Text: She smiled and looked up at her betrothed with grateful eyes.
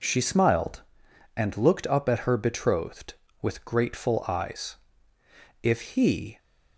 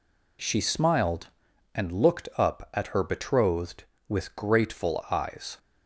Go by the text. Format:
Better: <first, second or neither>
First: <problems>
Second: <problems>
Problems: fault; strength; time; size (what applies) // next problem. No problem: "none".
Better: second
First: goes on to say "If he"; noticeable; from 5.6 s on; 0.76 s long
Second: none